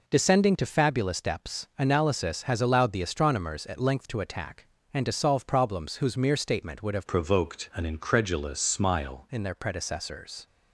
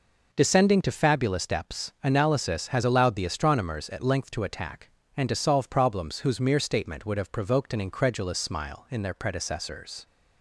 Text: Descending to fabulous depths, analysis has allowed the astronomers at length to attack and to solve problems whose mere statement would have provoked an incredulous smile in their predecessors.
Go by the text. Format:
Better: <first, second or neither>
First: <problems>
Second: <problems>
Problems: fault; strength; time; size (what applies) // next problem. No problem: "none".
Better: second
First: changes voice from "provoked" to "smile"; from 7.0 to 9.2 s; 2.2 s long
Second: none